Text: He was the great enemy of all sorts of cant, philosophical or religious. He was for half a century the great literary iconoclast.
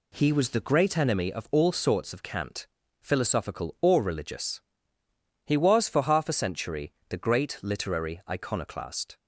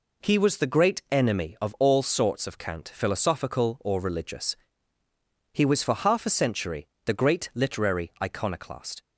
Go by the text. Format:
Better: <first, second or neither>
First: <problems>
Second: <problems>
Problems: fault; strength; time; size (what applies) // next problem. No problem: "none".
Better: neither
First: pauses between "century" and "the"; slight; at 6.9 s; 0.16 s long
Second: pauses between "century" and "the"; slight; at 6.8 s; 0.20 s long